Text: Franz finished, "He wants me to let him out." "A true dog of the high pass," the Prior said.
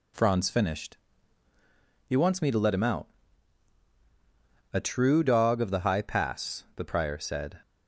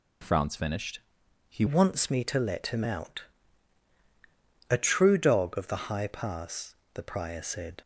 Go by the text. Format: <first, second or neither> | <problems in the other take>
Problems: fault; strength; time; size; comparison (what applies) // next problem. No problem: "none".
first | changes voice at "wants"; from 1.6 s on; 6.2 s long